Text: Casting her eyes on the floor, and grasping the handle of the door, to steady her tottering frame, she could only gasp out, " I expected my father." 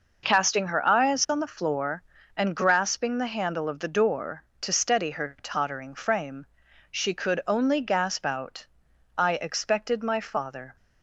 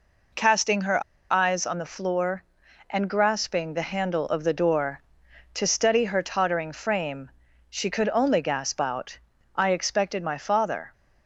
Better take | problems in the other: first | pauses between "her" and "eyes"; slight; at 1.0 s; 0.29 s long

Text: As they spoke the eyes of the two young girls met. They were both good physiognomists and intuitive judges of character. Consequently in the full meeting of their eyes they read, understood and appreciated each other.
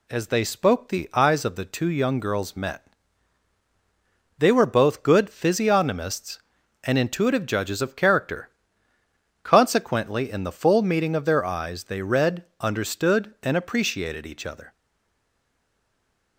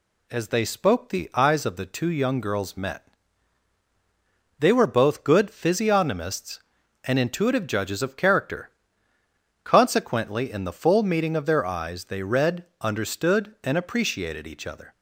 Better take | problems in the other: second | stays silent after the last word; noticeable; from 14.7 s on; 1.6 s long

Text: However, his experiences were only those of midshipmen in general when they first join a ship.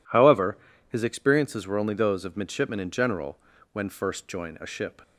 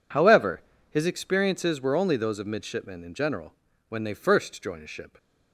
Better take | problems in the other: second | pauses between "general" and "when"; slight; at 3.3 s; 0.34 s long; slight in the second // skips "they"; at 3.8 s

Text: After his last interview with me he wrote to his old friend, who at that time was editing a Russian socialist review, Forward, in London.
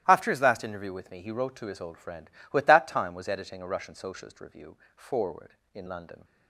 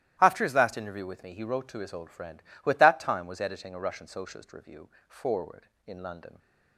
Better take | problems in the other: neither | starts louder than the rest; strong; the same in both

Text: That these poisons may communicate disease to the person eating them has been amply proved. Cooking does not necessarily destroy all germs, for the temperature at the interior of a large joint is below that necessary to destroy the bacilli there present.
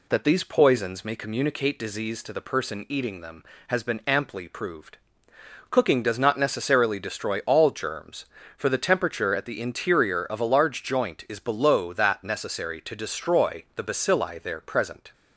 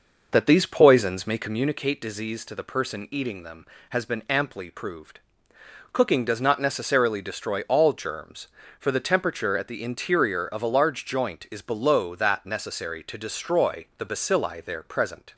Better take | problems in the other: first | starts louder than the rest; noticeable; until 1.7 s; 5.5 dB

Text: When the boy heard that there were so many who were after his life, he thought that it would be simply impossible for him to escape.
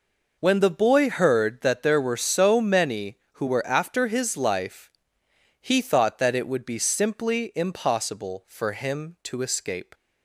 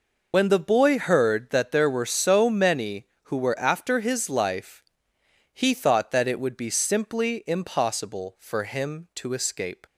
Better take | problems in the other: first | loses the start of "When"; at 0.3 s; 55 ms

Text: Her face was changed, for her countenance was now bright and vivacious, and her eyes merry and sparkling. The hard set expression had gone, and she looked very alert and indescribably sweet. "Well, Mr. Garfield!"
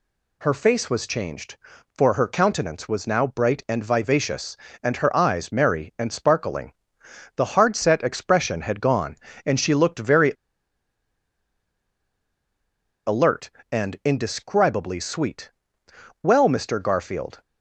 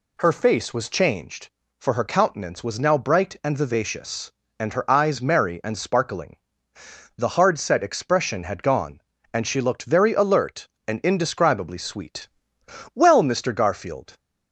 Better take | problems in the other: second | pauses between "very" and "alert"; strong; at 10.3 s; 2.7 s long

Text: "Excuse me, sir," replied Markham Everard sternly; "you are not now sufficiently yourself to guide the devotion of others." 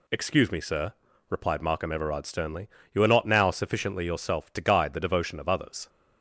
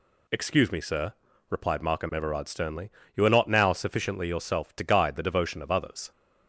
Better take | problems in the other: neither | none

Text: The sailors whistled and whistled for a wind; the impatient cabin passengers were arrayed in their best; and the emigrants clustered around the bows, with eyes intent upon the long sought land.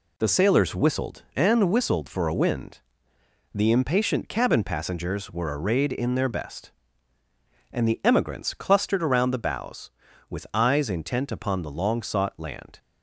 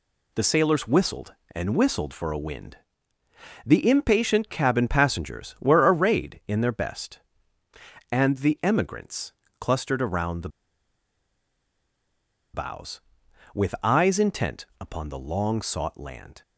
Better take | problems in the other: first | pauses between "emigrants" and "clustered"; slight; at 9.3 s; 0.26 s long // pauses between "the" and "bows"; strong; at 10.4 s; 2.0 s long // pauses between "intent" and "upon"; slight; at 14.6 s; 0.16 s long

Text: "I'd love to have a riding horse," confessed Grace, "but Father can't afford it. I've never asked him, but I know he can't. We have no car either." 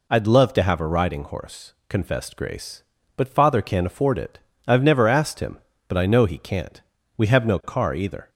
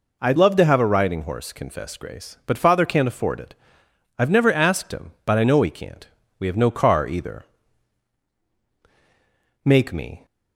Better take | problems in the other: first | goes on to say "Make me"; from 9.6 s on; 0.60 s long

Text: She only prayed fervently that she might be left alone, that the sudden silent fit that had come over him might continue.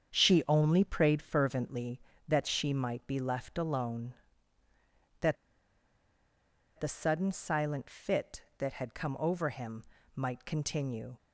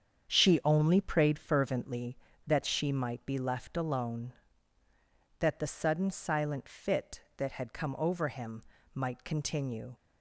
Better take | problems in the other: second | starts louder than the rest; strong; until 1.1 s; 7.5 dB; strong in the second // pauses between "that" and "the"; strong; at 5.3 s; 1.4 s long // pauses between "him" and "might"; slight; at 9.8 s; 0.32 s long; slight in the second

